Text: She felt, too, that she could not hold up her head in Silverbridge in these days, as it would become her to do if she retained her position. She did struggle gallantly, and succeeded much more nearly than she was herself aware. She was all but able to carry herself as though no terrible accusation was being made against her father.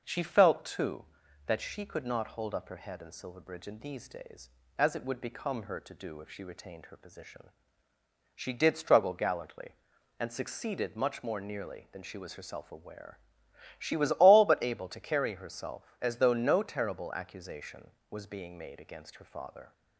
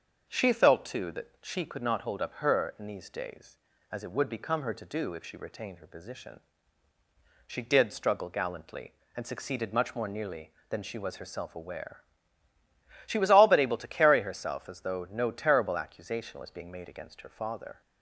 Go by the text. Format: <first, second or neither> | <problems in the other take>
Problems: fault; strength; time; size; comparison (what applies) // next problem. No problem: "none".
first | starts louder than the rest; until 1.3 s; 6.5 dB // skips "head in Silverbridge"; at 2.7 s